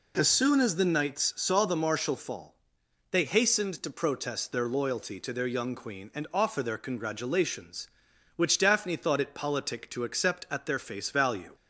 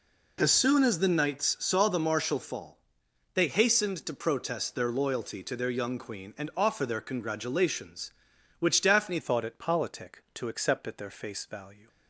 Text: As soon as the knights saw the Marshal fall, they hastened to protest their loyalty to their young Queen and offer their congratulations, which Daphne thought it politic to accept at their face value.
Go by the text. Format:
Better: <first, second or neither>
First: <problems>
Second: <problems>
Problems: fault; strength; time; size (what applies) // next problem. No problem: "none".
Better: first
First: none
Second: changes voice at "thought"; from 9.2 s on; 2.6 s long